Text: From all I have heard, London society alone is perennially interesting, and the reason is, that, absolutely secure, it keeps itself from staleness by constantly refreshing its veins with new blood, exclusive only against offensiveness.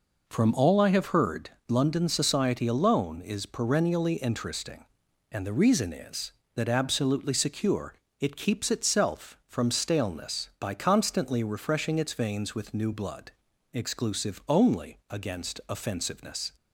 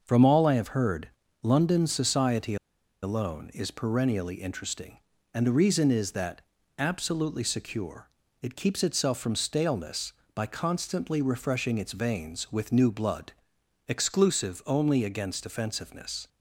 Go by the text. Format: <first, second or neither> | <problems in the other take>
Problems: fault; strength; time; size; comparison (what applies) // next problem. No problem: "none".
first | starts louder than the rest; noticeable; until 1.0 s; 6 dB // pauses between "society" and "alone"; noticeable; at 2.5 s; 0.47 s long